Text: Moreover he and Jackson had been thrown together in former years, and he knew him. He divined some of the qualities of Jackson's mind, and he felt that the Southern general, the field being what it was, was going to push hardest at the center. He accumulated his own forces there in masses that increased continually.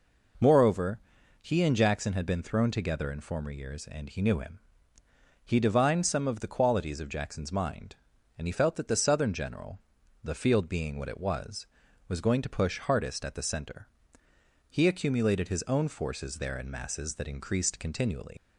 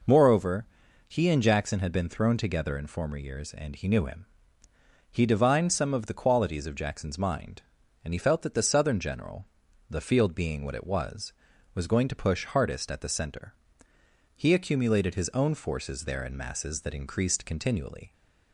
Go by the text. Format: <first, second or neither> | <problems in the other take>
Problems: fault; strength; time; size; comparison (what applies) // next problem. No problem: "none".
second | pauses between "Moreover" and "he"; at 0.9 s; 0.40 s long; also in the second // leaves "continually" unfinished; at 18.3 s; 90 ms